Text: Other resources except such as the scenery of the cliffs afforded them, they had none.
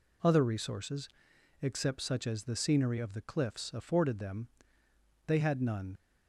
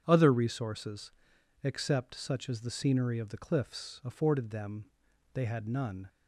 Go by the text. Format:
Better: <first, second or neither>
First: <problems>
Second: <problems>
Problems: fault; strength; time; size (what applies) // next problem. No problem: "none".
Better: second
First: pauses between "resources" and "except"; noticeable; at 1.0 s; 0.52 s long // leaves "none" unfinished; at 5.9 s; 40 ms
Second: pauses between "resources" and "except"; noticeable; at 1.1 s; 0.54 s long